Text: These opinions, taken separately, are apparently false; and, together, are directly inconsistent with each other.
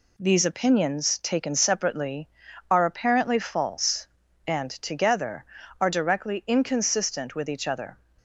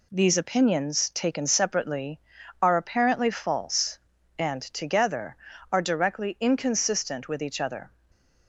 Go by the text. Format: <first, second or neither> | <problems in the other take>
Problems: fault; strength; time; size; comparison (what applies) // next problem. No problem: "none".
neither | none